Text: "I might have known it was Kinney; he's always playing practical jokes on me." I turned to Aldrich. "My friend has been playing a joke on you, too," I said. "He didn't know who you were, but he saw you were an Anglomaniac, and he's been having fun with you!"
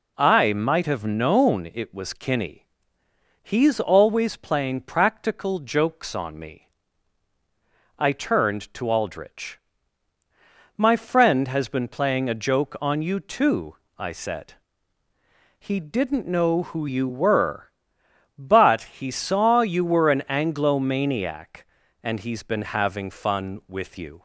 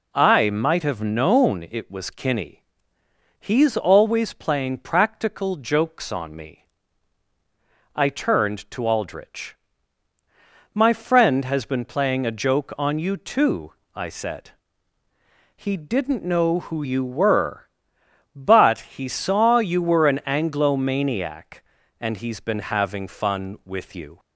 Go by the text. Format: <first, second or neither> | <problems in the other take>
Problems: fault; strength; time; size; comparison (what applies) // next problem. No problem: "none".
neither | none